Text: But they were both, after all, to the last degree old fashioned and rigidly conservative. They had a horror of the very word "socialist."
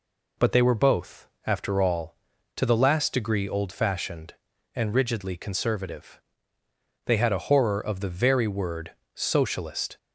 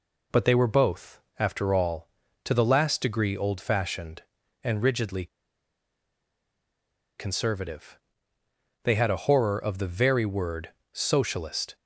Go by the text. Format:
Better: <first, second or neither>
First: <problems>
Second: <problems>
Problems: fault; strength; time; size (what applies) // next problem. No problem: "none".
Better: first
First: pauses between "word" and "socialist"; slight; at 8.9 s; 0.24 s long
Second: pauses between "rigidly" and "conservative"; strong; at 5.2 s; 1.9 s long // pauses between "word" and "socialist"; slight; at 10.6 s; 0.24 s long